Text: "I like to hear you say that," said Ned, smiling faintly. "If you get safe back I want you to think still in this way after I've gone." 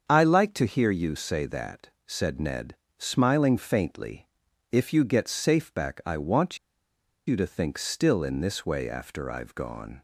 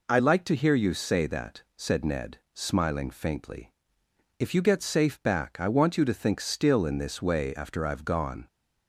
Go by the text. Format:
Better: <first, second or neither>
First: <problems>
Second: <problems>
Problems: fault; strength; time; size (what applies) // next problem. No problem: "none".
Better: second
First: starts louder than the rest; until 1.1 s; 7 dB // pauses between "want" and "you"; noticeable; at 6.5 s; 0.69 s long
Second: none